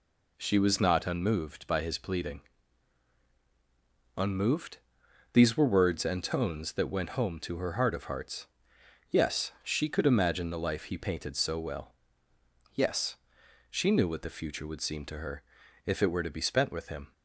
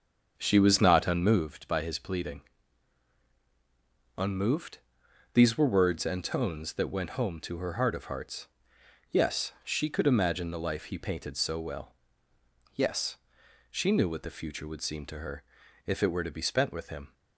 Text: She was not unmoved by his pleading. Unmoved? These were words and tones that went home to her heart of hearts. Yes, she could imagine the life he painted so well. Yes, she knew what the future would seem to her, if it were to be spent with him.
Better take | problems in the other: first | starts louder than the rest; until 1.5 s; 7 dB

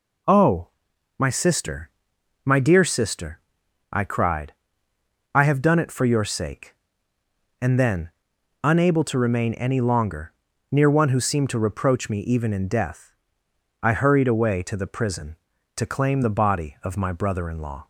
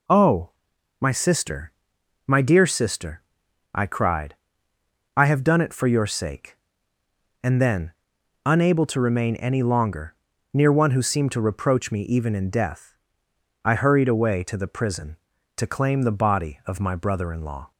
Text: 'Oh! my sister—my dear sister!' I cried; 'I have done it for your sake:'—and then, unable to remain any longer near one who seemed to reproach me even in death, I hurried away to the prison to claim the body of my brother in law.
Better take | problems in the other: neither | pauses between "longer" and "near"; the same in both

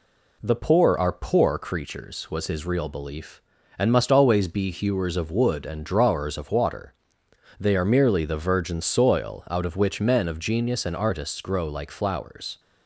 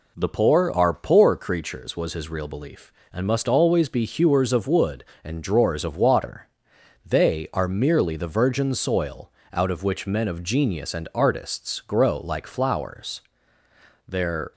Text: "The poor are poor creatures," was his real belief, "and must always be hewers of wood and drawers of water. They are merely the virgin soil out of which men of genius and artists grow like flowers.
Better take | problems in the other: first | pauses between "soil" and "out"; slight; at 9.3 s; 0.20 s long // goes on to say "Their"; slight; from 14.0 s on; 0.44 s long

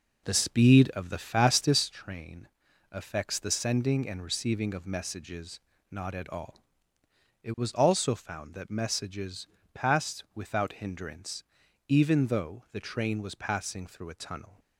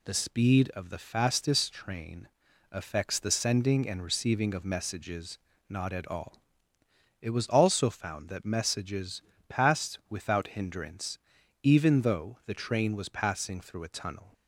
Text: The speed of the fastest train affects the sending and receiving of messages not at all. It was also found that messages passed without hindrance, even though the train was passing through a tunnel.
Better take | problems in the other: second | starts louder than the rest; noticeable; until 1.9 s; 4.5 dB // pauses between "train" and "affects"; at 2.4 s; 0.44 s long; also in the second // pauses between "messages" and "not"; slight; at 5.5 s; 0.32 s long; slight in the second // pauses between "messages" and "passed"; slight; at 9.4 s; 0.26 s long; slight in the second

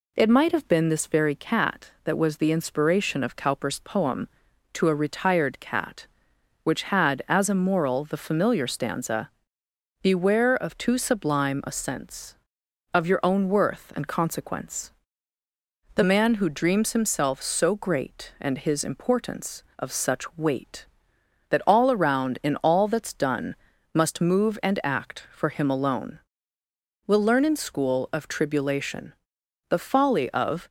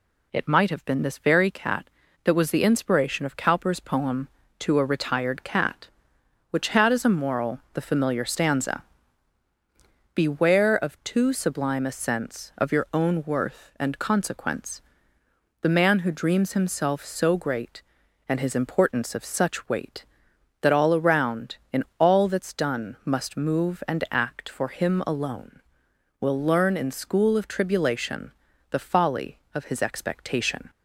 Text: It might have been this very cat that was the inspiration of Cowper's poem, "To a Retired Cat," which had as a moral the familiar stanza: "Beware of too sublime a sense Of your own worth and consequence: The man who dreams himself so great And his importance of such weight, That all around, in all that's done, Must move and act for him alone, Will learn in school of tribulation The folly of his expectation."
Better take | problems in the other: second | pauses between "tribulation" and "The"; noticeable; at 29.1 s; 0.58 s long; also in the second // stops before "his expectation"; at 30.6 s

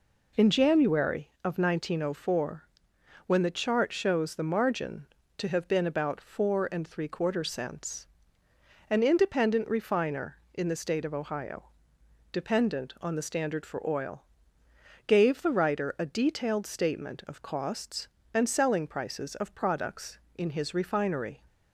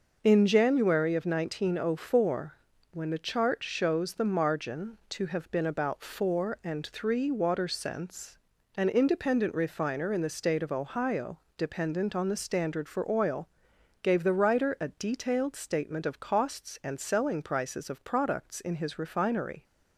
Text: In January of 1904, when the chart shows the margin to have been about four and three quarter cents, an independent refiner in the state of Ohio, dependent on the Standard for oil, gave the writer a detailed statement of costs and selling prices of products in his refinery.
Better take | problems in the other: first | says "water" for "quarter"; at 7.3 s

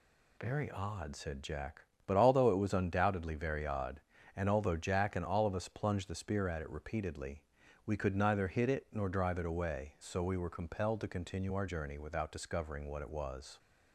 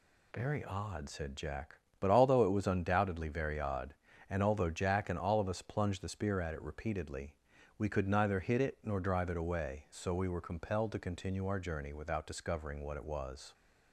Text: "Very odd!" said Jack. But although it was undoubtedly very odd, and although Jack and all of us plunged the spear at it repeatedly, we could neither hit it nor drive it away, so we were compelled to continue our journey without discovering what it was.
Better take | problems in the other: neither | none

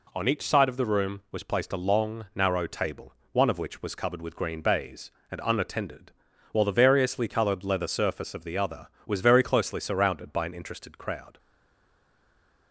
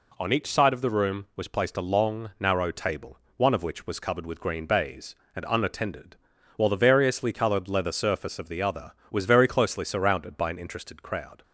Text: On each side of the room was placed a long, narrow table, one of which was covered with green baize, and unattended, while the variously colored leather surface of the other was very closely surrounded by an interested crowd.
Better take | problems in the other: second | stays silent after the last word; noticeable; from 11.3 s on; 1.4 s long

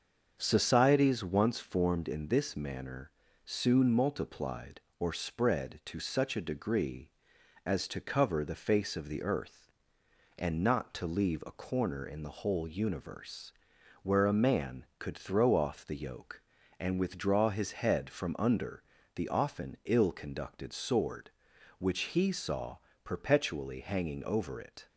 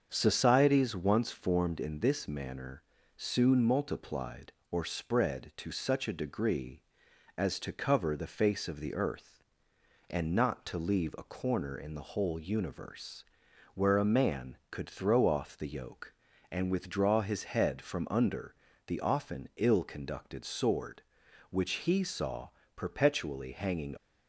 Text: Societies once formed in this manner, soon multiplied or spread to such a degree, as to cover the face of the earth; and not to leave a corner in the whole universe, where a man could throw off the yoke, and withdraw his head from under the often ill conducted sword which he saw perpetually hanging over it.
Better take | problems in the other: first | starts louder than the rest; until 1.1 s; 7 dB; also in the first // pauses between "under" and "the"; slight; at 18.5 s; 0.34 s long; slight in the first // pauses between "saw" and "perpetually"; slight; at 22.4 s; 0.26 s long; slight in the first // stops before "over it"; at 23.9 s

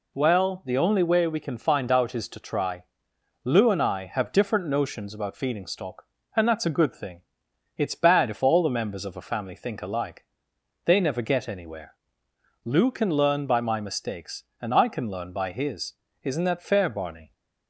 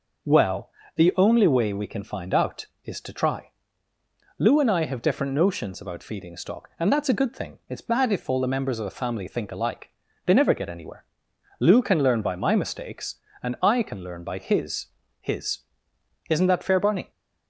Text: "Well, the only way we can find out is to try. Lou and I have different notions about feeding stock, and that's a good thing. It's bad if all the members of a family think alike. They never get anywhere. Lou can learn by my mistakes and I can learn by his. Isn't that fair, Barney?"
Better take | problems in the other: first | says "his" twice; at 15.1 s

